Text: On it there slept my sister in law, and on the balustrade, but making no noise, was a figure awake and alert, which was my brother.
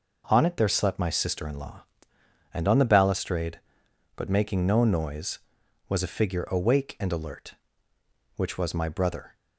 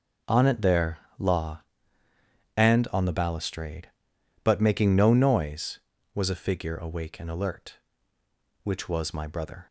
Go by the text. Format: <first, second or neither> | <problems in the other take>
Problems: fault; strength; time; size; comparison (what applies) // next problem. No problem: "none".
first | skips "slept my sister in"; at 1.0 s